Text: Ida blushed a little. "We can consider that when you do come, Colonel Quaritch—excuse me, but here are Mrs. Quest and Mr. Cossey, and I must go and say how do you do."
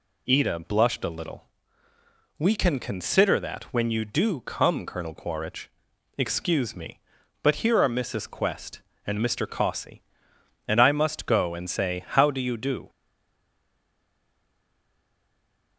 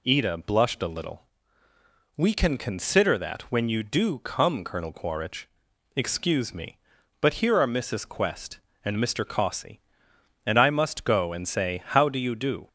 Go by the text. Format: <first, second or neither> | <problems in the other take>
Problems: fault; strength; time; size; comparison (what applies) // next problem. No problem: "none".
second | stays silent after the last word; strong; from 12.8 s on; 2.9 s long